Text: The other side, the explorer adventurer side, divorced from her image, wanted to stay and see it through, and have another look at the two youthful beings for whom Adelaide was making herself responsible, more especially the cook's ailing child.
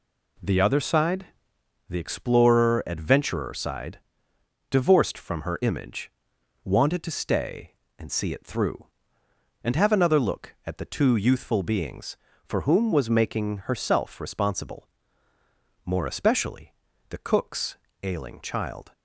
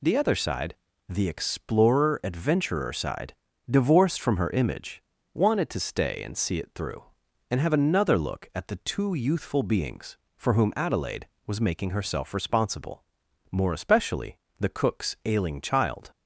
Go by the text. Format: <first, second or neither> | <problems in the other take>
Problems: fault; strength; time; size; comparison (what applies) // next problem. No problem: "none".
second | skips "Adelaide"; at 12.9 s // pauses between "especially" and "the"; at 16.7 s; 0.38 s long; slight in the second // pauses between "cook's" and "ailing"; slight; at 17.7 s; 0.26 s long